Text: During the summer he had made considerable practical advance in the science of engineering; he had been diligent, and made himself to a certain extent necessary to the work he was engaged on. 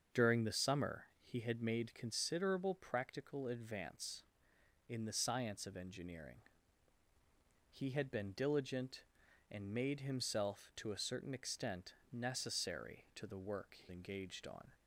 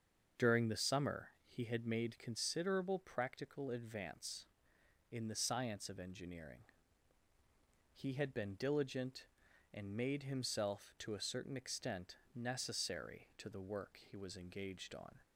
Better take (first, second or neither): second